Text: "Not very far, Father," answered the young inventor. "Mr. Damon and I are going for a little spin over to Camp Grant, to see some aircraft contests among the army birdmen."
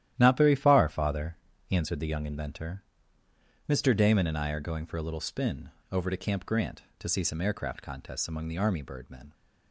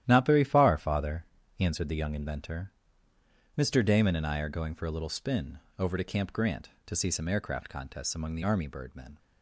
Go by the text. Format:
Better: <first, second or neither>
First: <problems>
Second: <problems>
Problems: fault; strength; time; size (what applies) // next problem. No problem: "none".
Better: neither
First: starts louder than the rest; strong; until 1.1 s; 12 dB // pauses between "spin" and "over"; slight; at 5.7 s; 0.19 s long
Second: starts louder than the rest; strong; until 1.0 s; 12 dB // pauses between "spin" and "over"; slight; at 5.5 s; 0.18 s long